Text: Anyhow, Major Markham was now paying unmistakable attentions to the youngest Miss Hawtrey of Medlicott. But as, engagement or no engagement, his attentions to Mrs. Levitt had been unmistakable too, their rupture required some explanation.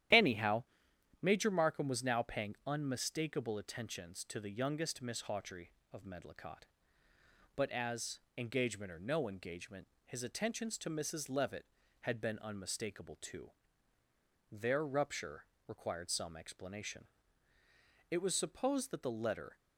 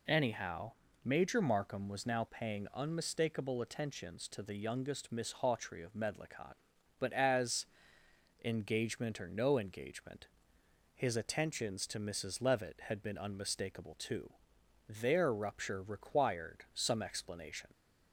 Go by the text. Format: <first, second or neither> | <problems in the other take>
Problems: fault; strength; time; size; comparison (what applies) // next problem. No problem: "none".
second | starts louder than the rest; strong; until 1.7 s; 12 dB // pauses between "rupture" and "required"; slight; at 15.4 s; 0.20 s long // goes on to say "It was supposed that the letter"; from 18.0 s on; 1.4 s long